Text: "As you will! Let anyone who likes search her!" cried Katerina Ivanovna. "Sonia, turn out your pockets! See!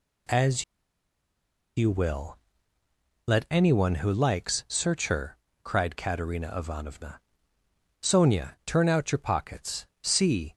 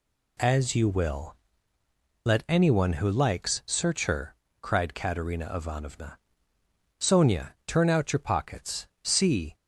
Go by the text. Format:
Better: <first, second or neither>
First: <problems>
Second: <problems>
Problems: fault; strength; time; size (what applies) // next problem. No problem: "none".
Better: second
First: pauses between "As" and "you"; at 0.6 s; 1.1 s long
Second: none